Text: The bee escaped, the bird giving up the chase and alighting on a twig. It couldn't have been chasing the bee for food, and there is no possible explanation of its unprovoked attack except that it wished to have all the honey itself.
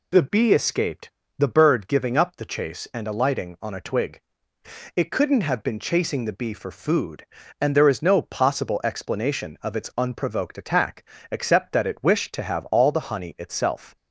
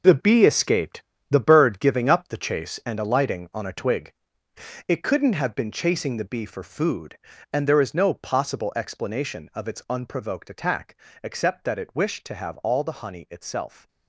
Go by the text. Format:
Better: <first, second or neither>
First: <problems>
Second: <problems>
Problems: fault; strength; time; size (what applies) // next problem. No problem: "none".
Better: first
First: pauses between "attack" and "except"; slight; at 11.0 s; 0.28 s long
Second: gets quieter; strong; throughout; 10 dB // pauses between "attack" and "except"; slight; at 10.9 s; 0.28 s long